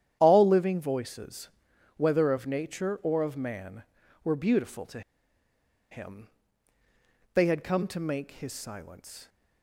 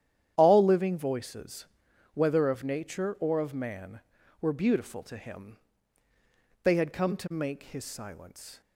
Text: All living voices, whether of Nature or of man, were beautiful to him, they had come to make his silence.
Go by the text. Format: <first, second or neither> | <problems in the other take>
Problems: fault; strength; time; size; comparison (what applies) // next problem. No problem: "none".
second | starts louder than the rest; strong; until 1.2 s; 10 dB; strong in the second // pauses between "to" and "him"; noticeable; at 5.0 s; 0.90 s long